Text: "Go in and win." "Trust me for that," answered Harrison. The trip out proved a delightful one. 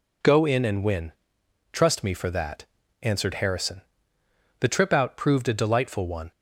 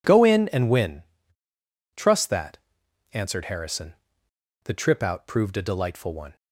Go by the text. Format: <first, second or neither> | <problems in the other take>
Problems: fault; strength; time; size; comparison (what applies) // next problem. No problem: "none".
first | skips "me for"; at 2.2 s